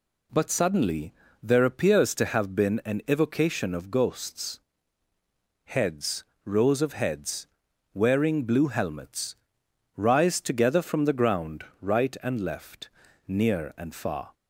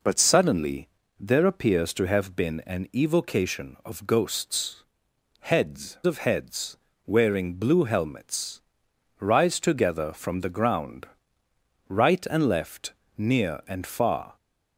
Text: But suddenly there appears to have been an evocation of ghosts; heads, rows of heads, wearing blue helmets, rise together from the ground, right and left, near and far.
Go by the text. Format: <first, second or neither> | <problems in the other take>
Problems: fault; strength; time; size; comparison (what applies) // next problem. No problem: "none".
first | pauses between "suddenly" and "there"; slight; at 0.8 s; 0.30 s long; slight in the first // skips "rows"; at 6.0 s